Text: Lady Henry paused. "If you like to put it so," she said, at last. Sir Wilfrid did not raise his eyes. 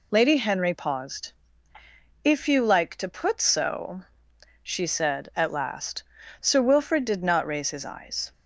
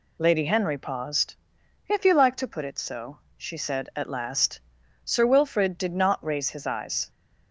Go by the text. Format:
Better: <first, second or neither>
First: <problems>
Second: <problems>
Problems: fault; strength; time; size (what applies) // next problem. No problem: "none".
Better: second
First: skips "it"; at 3.3 s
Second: none